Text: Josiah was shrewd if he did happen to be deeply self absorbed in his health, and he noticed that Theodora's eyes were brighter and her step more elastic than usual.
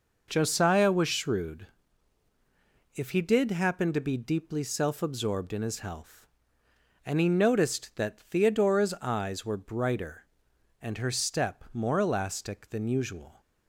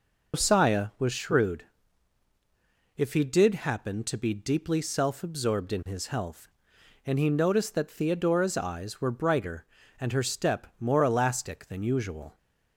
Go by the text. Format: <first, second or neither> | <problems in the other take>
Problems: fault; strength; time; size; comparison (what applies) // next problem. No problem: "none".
first | loses the start of "Josiah"; at 0.3 s; 170 ms // pauses between "shrewd" and "if"; strong; at 1.6 s; 1.3 s long; strong in the first